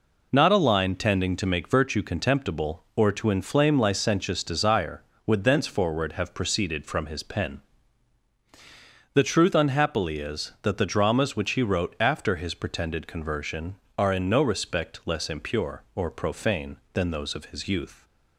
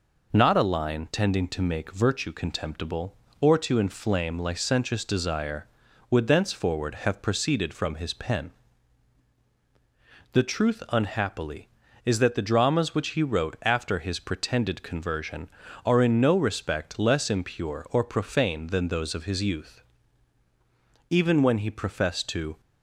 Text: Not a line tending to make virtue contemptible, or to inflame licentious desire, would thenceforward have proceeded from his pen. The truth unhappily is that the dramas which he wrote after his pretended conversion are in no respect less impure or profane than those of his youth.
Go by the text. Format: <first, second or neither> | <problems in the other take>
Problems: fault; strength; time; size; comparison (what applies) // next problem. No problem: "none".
first | goes on to say "Even when he professed to"; from 21.0 s on; 1.5 s long